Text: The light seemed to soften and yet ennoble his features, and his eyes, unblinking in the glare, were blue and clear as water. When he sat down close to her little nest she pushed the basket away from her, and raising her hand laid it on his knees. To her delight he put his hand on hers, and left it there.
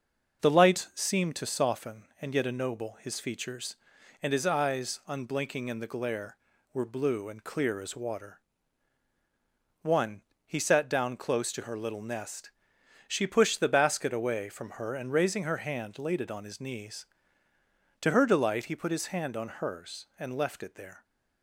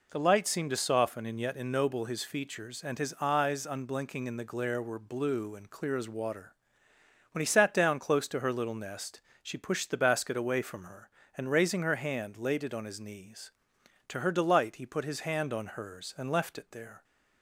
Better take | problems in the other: second | starts louder than the rest; noticeable; until 1.4 s; 6 dB // says "One" for "When"; at 9.8 s // pauses between "nest" and "she"; noticeable; at 12.4 s; 0.58 s long; slight in the second

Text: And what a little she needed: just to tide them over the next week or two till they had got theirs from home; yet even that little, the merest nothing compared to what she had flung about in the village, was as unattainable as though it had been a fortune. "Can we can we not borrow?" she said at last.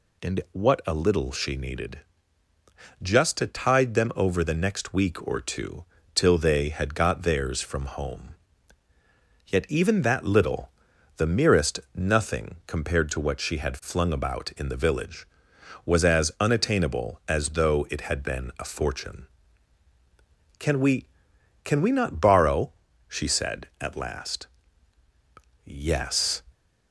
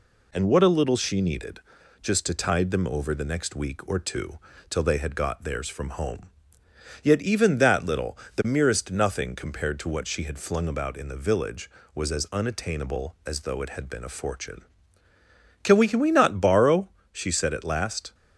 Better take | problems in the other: second | pauses between "two" and "till"; slight; at 5.8 s; 0.32 s long; slight in the second // goes on to say "Yes"; noticeable; from 25.6 s on; 0.78 s long

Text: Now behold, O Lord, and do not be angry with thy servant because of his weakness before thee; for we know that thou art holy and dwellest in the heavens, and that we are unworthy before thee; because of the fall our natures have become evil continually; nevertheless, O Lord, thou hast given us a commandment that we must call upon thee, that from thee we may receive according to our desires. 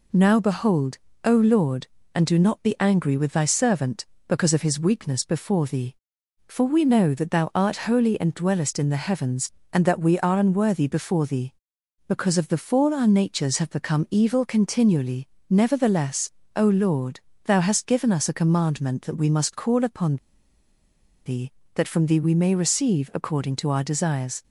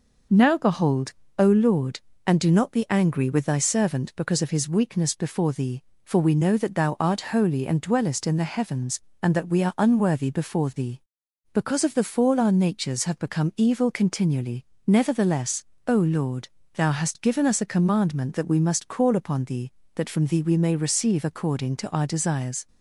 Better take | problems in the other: second | pauses between "upon" and "thee"; at 20.1 s; 1.0 s long

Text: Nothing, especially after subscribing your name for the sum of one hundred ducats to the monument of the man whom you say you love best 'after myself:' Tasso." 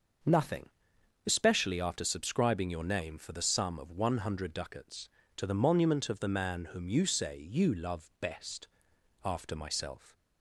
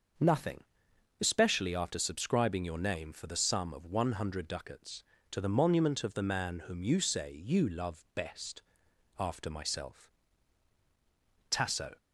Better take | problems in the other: second | starts louder than the rest; until 1.8 s; 6 dB; also in the second // pauses between "best" and "after"; noticeable; at 8.6 s; 0.56 s long; noticeable in the second // stops before "Tasso"; at 10.1 s

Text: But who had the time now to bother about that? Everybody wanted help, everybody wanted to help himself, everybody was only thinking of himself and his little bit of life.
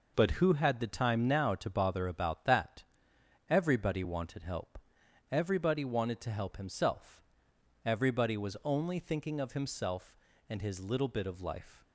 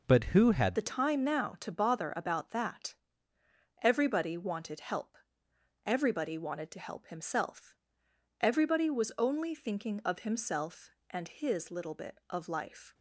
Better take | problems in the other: first | changes voice at "the"; from 0.7 s on; 12.2 s long

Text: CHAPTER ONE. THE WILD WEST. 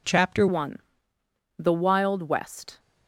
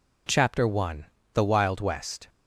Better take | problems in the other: second | changes voice at "ONE"; from 0.4 s on; 2.3 s long

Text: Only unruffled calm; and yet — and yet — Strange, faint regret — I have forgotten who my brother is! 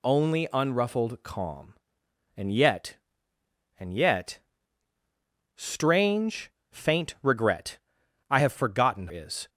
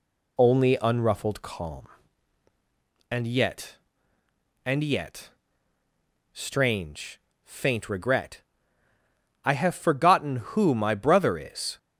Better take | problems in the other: second | skips "who my brother"; at 9.0 s

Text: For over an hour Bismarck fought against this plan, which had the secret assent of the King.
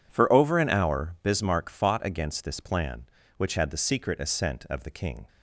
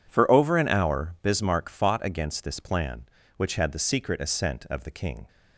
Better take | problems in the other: neither | none

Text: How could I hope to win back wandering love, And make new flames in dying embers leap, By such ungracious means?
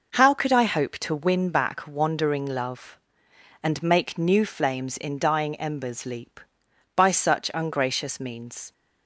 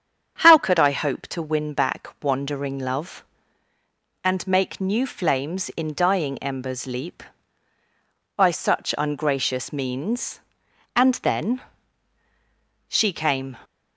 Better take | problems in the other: first | starts louder than the rest; strong; until 1.4 s; 7.5 dB // goes on to say "And then She came"; strong; from 10.9 s on; 2.6 s long

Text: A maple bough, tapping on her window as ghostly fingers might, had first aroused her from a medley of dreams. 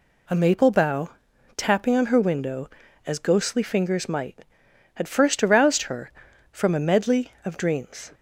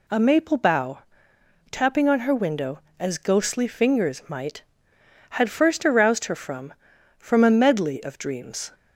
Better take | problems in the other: first | says "from" twice; at 7.1 s

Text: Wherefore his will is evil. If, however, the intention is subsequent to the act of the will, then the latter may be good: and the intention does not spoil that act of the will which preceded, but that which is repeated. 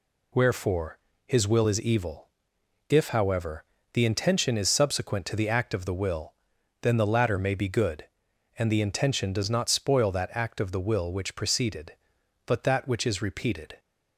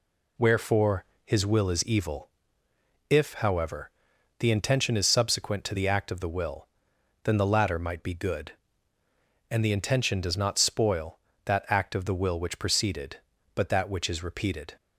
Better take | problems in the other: first | pauses between "Wherefore" and "his"; slight; at 1.0 s; 0.20 s long; slight in the first // says "might" for "may"; at 7.7 s

